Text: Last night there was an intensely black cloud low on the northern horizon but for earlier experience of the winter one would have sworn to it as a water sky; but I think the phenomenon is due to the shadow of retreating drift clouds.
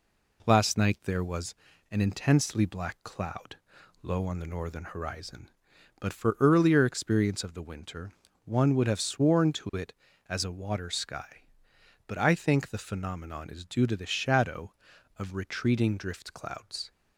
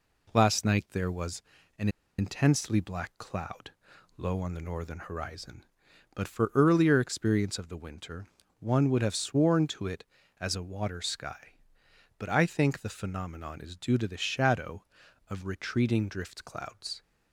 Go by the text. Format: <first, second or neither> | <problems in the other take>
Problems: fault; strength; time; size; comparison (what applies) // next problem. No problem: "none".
first | pauses between "was" and "an"; at 1.4 s; 0.38 s long; also in the first // pauses between "an" and "intensely"; slight; at 1.8 s; 0.30 s long // pauses between "cloud" and "low"; at 3.7 s; 0.44 s long; also in the first // pauses between "winter" and "one"; slight; at 8.2 s; 0.36 s long; slight in the first